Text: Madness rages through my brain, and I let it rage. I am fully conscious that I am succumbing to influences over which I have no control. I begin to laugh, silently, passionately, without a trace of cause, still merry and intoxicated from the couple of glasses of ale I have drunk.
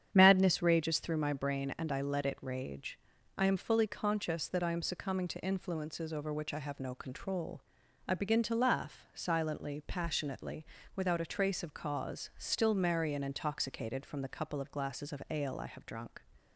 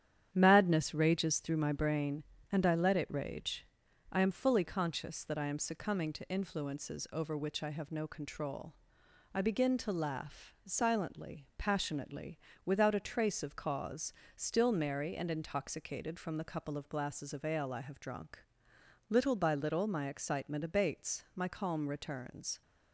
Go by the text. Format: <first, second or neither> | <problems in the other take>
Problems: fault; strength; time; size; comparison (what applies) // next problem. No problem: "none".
first | starts louder than the rest; strong; until 1.3 s; 9.5 dB; strong in the first // goes on to say "Little by little my excitement abates my calm returns"; strong; from 19.0 s on; 3.5 s long